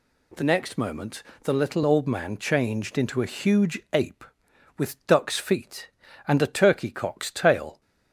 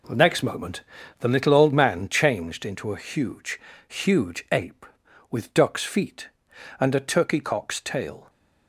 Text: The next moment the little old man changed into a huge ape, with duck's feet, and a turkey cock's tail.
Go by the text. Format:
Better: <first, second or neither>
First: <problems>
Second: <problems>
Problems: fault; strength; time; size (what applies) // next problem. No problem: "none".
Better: first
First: pauses between "moment" and "the"; slight; at 1.2 s; 0.18 s long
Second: pauses between "moment" and "the"; at 0.8 s; 0.38 s long // says "huge" twice; at 3.8 s